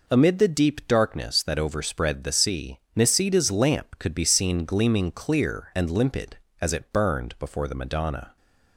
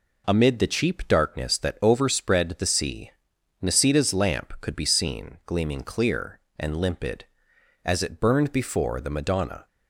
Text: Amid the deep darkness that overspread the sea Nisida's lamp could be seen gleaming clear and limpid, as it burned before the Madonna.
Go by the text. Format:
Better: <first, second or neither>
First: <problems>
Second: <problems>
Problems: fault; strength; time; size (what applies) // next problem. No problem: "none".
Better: first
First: pauses between "sea" and "Nisida's"; slight; at 2.7 s; 0.16 s long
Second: says "cheap" for "deep"; at 0.6 s // pauses between "sea" and "Nisida's"; noticeable; at 3.1 s; 0.50 s long